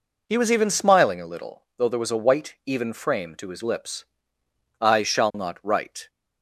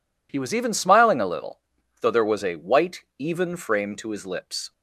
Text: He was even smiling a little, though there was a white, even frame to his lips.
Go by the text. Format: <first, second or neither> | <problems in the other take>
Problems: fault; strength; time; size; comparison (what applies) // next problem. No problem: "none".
second | goes on to say "I shall not write"; noticeable; from 4.7 s on; 1.2 s long